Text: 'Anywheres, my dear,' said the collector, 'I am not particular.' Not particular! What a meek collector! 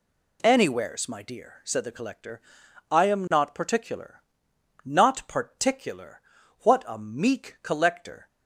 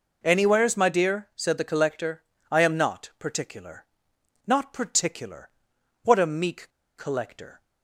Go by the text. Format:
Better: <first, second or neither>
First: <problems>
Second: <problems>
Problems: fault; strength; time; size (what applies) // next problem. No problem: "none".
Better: first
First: none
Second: pauses between "meek" and "collector"; slight; at 6.6 s; 0.27 s long